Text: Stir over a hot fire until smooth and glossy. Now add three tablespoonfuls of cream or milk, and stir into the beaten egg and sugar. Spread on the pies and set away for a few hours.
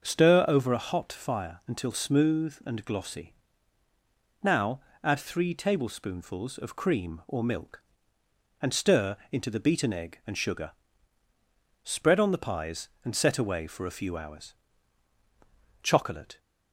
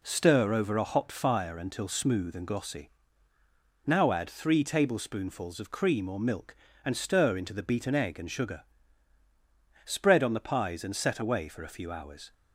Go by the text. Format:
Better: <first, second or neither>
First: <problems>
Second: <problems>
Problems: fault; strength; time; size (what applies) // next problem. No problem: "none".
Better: second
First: starts louder than the rest; until 1.0 s; 6.5 dB // pauses between "Now" and "add"; slight; at 4.8 s; 0.24 s long // goes on to say "CHOCOLATE"; from 15.8 s on; 0.54 s long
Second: none